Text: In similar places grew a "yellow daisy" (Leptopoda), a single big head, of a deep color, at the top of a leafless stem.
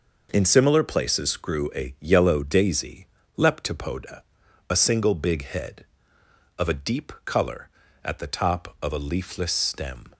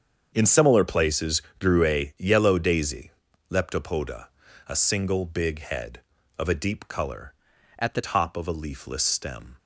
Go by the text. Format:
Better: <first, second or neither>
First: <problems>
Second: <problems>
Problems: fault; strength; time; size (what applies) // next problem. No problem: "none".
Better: first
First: none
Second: starts louder than the rest; strong; until 1.3 s; 7 dB // pauses between "places" and "grew"; slight; at 1.4 s; 0.16 s long // changes voice from "at" to "the"; from 7.7 to 8.0 s; 0.3 s long